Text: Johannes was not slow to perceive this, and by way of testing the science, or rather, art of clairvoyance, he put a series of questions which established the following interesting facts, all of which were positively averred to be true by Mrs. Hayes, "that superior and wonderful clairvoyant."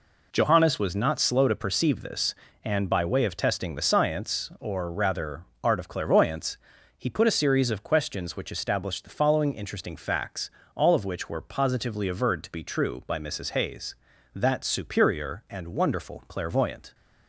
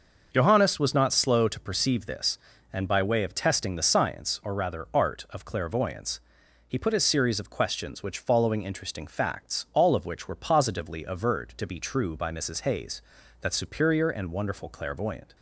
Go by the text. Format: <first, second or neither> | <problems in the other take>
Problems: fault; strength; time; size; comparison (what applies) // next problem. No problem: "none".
first | starts louder than the rest; until 1.3 s; 6 dB // skips "established the"; at 8.1 s